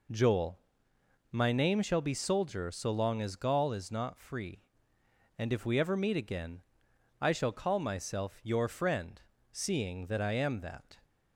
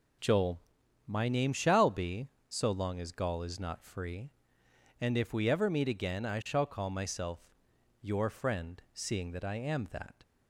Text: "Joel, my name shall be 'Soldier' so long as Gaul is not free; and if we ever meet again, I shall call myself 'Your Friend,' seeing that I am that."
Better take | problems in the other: first | skips "Soldier"; at 2.3 s // pauses between "myself" and "Your"; noticeable; at 7.5 s; 0.50 s long

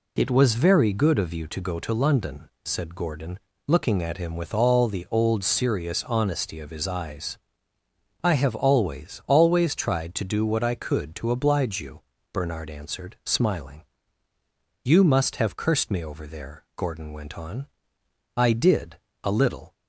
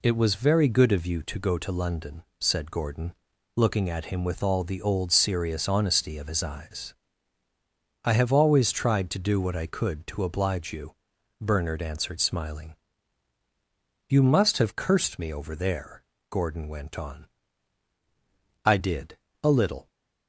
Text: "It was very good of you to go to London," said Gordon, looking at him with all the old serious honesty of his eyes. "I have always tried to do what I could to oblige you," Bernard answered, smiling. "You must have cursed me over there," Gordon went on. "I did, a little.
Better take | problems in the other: second | says "always" twice; at 9.2 s

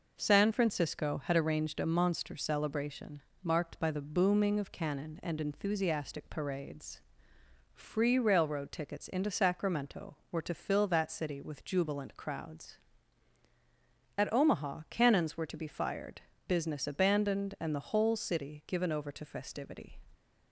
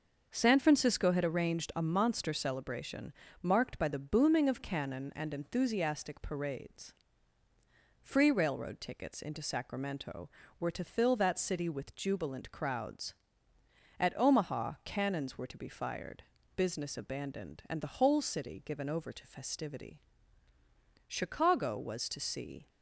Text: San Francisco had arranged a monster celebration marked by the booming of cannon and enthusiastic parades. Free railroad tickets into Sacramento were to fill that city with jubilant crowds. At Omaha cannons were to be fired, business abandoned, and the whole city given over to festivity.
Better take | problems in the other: first | starts louder than the rest; until 1.3 s; 6 dB // pauses between "celebration" and "marked"; slight; at 3.1 s; 0.28 s long; slight in the first // goes on to say "Chicago was to see"; from 21.0 s on; 1.6 s long

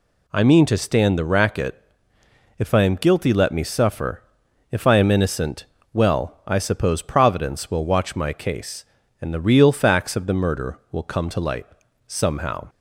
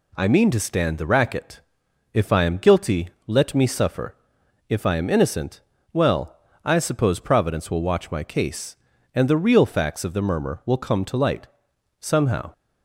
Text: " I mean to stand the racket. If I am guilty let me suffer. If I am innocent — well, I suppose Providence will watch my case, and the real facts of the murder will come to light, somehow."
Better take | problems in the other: first | pauses between "guilty" and "let"; slight; at 3.0 s; 0.18 s long // says "murmur" for "murder"; at 10.2 s

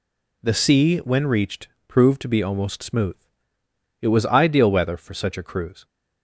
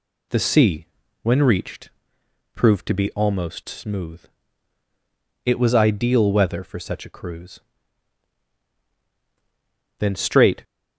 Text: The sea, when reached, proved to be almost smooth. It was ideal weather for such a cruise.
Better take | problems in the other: first | goes on to say "Then straight"; noticeable; from 9.9 s on; 0.64 s long

